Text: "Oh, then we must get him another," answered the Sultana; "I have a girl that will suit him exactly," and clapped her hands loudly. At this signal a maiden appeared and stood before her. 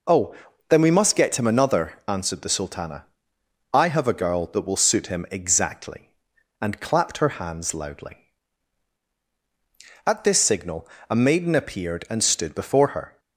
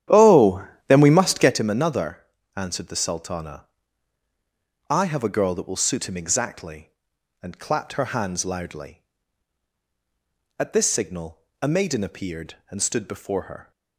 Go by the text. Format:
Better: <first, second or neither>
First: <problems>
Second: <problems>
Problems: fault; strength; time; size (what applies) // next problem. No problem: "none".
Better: first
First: pauses between "signal" and "a"; slight; at 10.8 s; 0.22 s long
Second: starts louder than the rest; strong; until 1.7 s; 10.5 dB // pauses between "signal" and "a"; slight; at 11.4 s; 0.20 s long